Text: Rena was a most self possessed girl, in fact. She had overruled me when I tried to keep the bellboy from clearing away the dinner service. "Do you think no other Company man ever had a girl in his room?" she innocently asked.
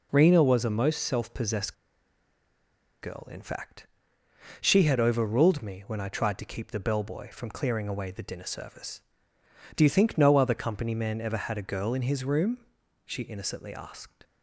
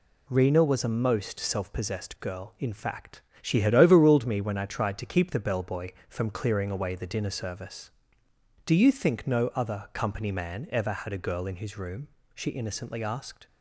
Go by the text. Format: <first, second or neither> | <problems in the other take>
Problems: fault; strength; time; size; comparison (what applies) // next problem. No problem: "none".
second | pauses between "possessed" and "girl"; strong; at 1.7 s; 1.2 s long